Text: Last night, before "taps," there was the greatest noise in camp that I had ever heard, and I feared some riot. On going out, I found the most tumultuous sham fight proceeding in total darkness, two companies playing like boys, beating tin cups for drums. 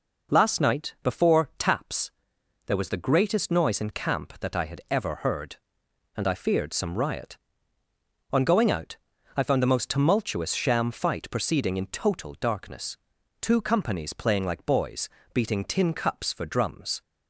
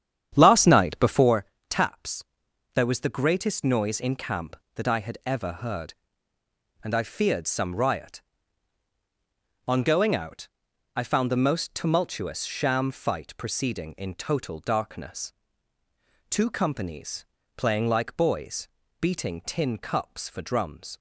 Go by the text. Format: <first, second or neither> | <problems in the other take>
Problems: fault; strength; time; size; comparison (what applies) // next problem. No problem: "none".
first | starts louder than the rest; strong; until 1.4 s; 9.5 dB // pauses between "before" and "taps"; slight; at 1.4 s; 0.24 s long // pauses between "companies" and "playing"; slight; at 17.2 s; 0.32 s long